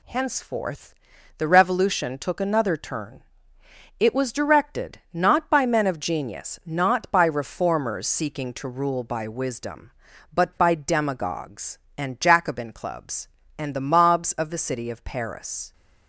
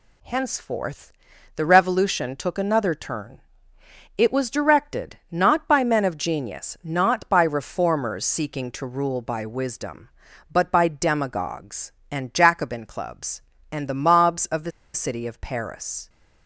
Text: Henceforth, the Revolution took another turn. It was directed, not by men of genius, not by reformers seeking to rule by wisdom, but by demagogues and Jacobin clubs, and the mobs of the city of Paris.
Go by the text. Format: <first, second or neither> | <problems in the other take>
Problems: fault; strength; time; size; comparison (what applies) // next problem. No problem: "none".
first | pauses between "the" and "city"; slight; at 14.7 s; 0.24 s long